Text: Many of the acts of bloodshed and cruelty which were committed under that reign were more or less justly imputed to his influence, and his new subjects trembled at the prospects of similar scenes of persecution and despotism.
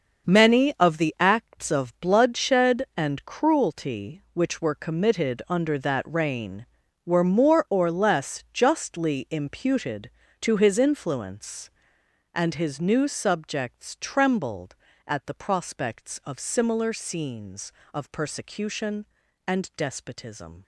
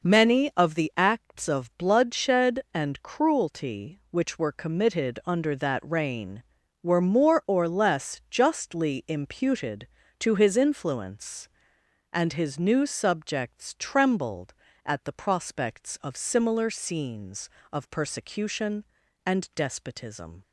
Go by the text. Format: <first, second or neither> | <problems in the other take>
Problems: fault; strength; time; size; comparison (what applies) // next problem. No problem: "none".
second | gets quieter; strong; throughout; 10.5 dB